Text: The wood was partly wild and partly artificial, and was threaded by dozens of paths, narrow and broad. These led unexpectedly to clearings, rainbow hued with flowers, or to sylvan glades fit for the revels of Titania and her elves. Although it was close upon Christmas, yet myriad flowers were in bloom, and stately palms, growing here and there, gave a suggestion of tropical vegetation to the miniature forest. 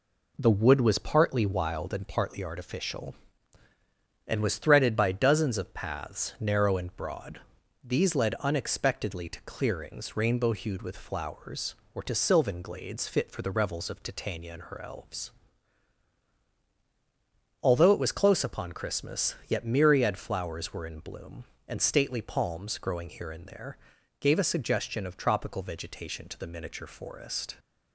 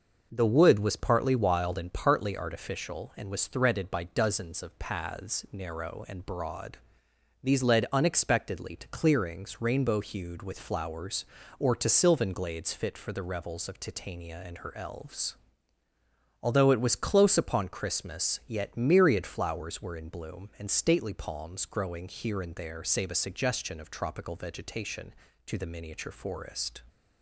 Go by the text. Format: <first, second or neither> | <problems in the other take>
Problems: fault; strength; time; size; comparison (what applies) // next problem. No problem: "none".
first | says "save" for "gave"; at 22.8 s